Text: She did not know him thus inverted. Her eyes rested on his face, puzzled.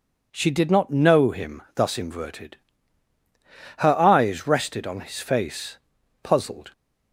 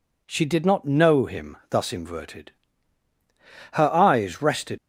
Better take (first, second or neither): first